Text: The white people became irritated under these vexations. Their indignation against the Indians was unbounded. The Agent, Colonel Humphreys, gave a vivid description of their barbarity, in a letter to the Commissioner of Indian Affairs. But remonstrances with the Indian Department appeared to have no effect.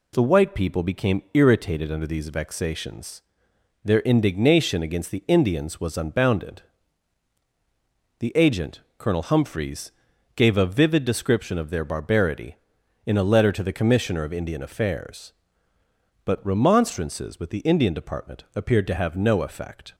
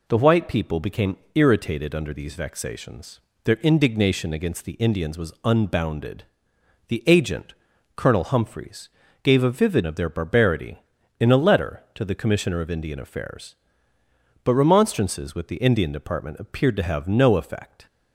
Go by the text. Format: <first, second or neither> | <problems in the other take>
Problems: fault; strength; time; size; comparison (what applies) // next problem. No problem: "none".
first | pauses between "became" and "irritated"; slight; at 1.1 s; 0.18 s long // skips "description"; at 9.8 s